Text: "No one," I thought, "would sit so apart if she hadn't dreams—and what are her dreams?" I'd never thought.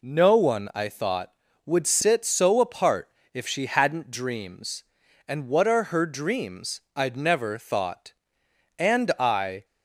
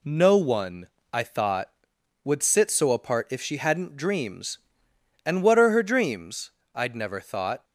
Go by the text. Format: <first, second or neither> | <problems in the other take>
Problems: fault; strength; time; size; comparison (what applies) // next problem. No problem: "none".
second | pauses between "apart" and "if"; slight; at 3.1 s; 0.22 s long // goes on to say "And I"; noticeable; from 8.7 s on; 0.88 s long